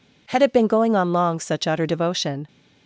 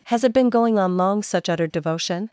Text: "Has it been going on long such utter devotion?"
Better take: second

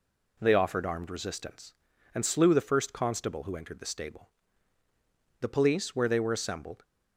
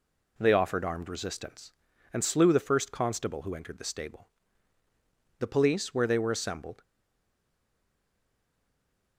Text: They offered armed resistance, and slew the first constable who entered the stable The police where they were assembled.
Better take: first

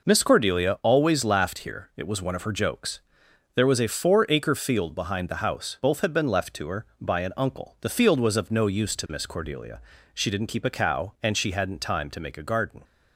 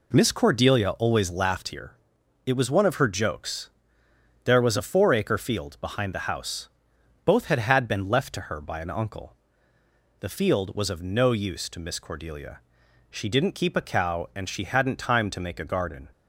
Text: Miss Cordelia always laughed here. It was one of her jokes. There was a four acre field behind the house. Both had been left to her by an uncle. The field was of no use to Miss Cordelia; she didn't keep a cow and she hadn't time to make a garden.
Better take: first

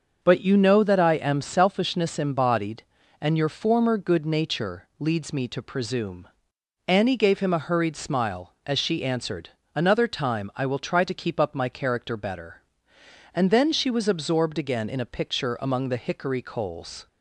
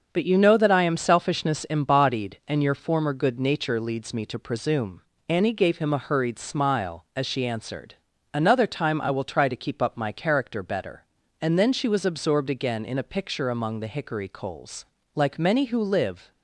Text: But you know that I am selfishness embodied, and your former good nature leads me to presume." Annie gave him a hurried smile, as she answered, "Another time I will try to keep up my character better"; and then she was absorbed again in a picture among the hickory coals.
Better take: first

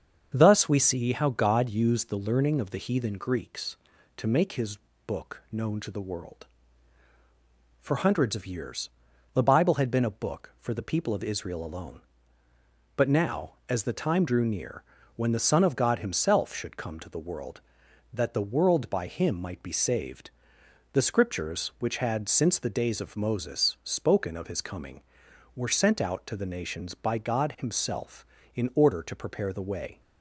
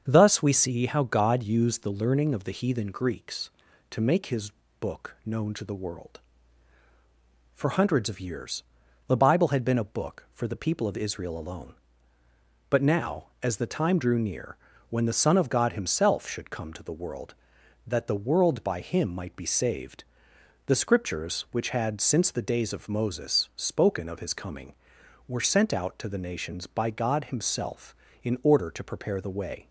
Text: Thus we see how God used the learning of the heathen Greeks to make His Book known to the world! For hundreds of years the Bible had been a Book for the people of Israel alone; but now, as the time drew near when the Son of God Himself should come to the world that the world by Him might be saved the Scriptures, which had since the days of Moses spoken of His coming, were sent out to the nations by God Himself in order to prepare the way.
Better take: neither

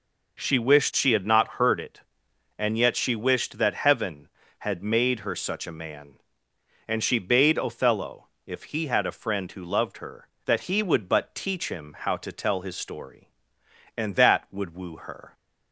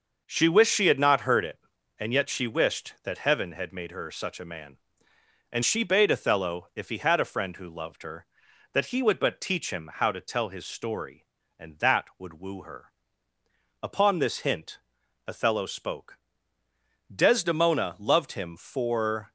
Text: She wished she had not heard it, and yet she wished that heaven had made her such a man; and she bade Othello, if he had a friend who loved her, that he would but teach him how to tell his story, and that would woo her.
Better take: first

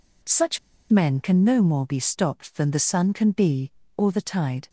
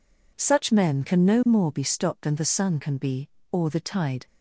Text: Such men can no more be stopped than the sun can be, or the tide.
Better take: second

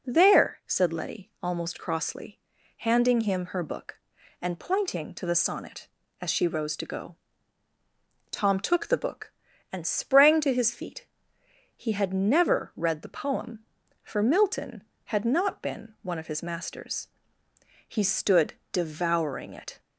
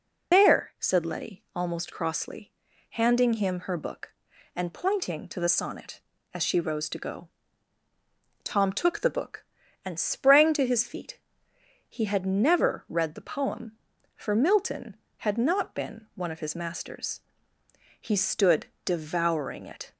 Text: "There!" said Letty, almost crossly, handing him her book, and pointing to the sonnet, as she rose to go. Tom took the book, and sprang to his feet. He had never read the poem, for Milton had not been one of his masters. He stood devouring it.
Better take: first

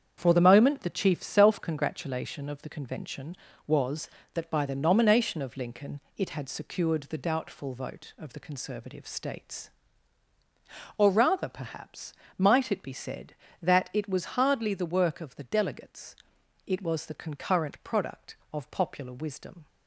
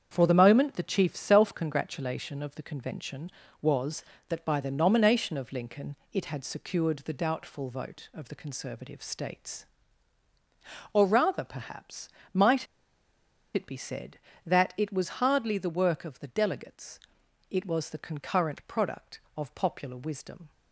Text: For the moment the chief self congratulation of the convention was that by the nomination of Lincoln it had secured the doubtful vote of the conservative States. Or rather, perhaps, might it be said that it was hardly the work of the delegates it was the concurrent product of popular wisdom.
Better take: first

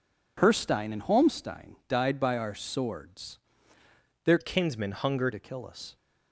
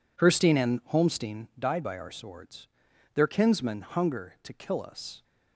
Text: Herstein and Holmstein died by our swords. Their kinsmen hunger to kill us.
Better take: second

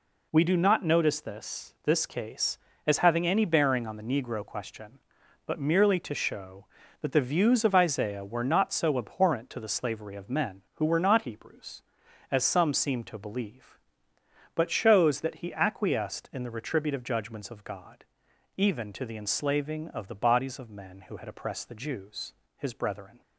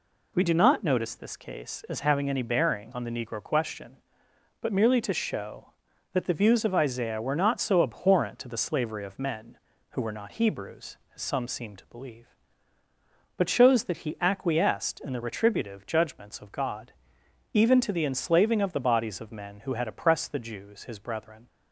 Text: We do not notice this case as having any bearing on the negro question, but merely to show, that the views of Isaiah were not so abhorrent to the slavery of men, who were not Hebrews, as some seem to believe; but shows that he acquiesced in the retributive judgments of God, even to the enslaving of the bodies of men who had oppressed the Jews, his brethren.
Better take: second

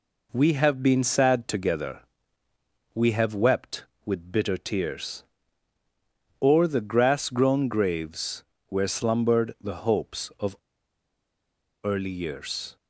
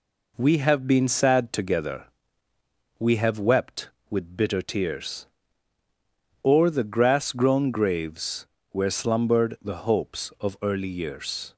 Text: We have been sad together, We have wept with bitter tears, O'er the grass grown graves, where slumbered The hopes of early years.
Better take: second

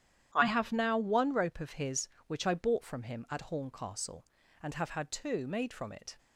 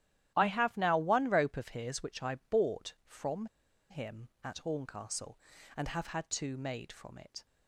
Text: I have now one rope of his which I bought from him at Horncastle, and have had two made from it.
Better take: first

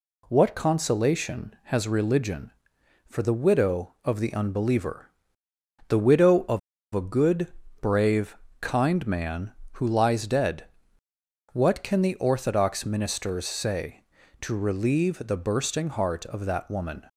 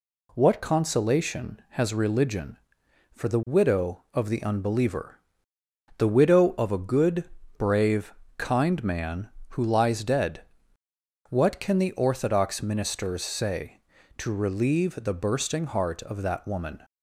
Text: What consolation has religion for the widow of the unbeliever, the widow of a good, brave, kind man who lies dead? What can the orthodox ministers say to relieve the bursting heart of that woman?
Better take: second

